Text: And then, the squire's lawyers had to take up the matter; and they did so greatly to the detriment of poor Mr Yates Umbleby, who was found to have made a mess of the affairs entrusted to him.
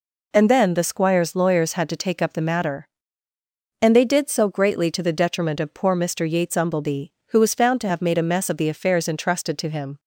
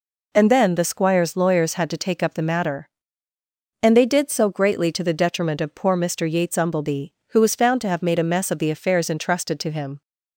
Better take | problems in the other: neither | none

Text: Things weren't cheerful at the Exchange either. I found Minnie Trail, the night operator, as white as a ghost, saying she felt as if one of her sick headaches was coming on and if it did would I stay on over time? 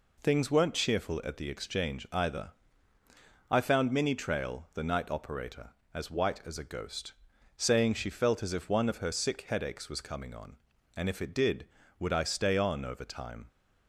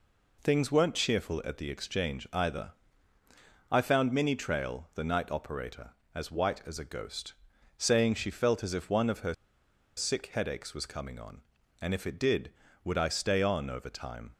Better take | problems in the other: first | pauses between "her" and "sick"; noticeable; at 9.3 s; 0.63 s long

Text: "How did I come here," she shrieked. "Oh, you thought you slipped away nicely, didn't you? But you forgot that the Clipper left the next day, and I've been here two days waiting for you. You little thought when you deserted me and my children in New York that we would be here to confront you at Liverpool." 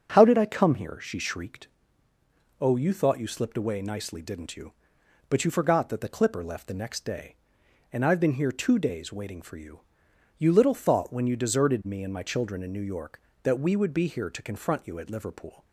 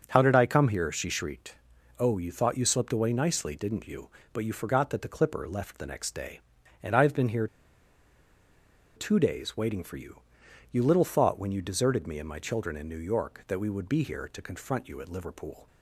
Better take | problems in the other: first | starts louder than the rest; until 1.0 s; 6.5 dB; also in the first // pauses between "here" and "two"; strong; at 7.4 s; 1.4 s long

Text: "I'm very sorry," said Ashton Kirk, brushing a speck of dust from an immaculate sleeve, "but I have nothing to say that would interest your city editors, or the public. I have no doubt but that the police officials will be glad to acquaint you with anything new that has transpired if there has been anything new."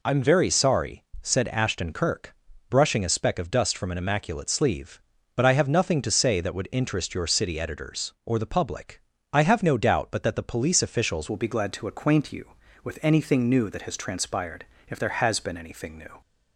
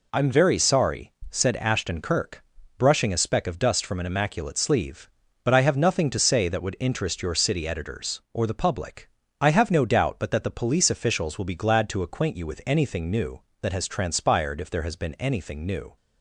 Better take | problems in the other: second | changes voice at "will"; from 11.3 s on; 4.9 s long // pauses between "transpired" and "if"; slight; at 14.6 s; 0.22 s long

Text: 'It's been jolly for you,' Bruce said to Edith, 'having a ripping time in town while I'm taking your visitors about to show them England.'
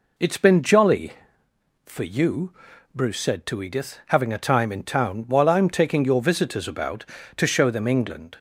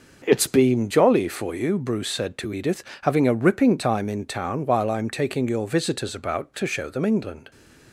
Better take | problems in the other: second | skips "ripping"; at 4.3 s

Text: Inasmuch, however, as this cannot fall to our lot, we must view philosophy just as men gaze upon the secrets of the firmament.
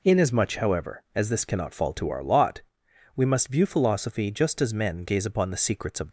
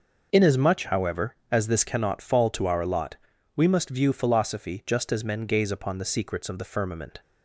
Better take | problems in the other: second | stops before "the firmament"; at 6.0 s

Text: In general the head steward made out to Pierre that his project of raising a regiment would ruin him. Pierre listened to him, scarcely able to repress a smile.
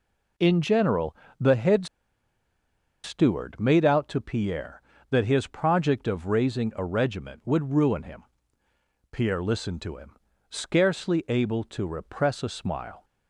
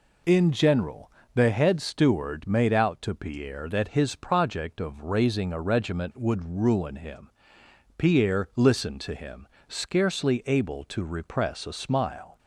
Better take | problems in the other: second | pauses between "general" and "the"; slight; at 1.1 s; 0.24 s long; slight in the second // pauses between "head" and "steward"; at 1.8 s; 1.1 s long

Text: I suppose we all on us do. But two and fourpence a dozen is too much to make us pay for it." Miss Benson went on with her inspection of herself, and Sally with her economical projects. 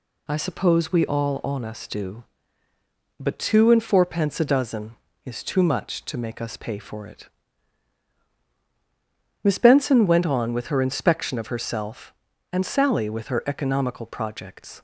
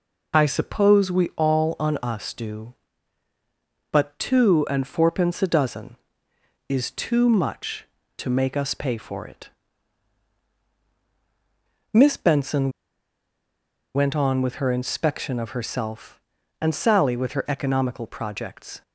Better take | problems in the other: first | pauses between "Benson" and "went"; at 12.7 s; 1.2 s long

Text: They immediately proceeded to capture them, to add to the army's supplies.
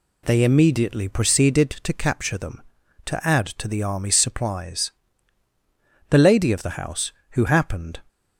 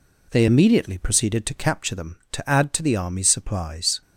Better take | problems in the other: second | goes on to say "The lady of the house who happened"; strong; from 6.1 s on; 1.9 s long

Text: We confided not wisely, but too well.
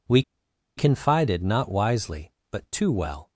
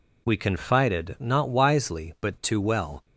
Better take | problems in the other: second | pauses between "We" and "confided"; noticeable; at 0.2 s; 0.54 s long

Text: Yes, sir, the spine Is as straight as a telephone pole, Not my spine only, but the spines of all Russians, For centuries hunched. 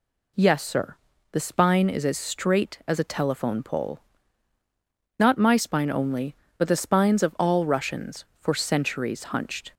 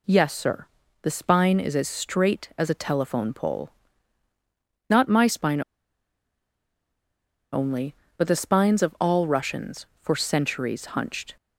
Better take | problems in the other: first | pauses between "spine" and "only"; strong; at 5.6 s; 1.9 s long

